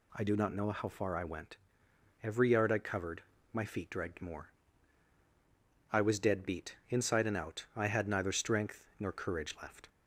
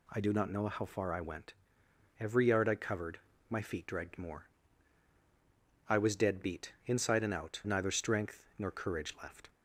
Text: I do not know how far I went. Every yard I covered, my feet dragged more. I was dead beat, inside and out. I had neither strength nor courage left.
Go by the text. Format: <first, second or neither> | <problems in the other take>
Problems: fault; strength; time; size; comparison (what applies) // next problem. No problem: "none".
first | skips "I had"; at 7.6 s